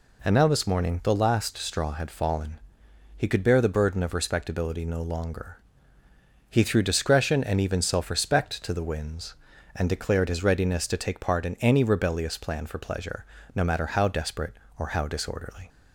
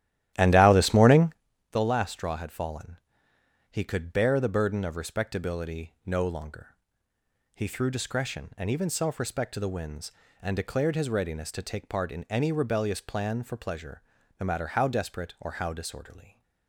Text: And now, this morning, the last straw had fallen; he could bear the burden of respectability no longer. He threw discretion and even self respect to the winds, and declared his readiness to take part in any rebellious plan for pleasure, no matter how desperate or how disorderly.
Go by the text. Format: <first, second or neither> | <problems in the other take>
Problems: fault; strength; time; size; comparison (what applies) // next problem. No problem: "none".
first | starts louder than the rest; strong; until 1.4 s; 13 dB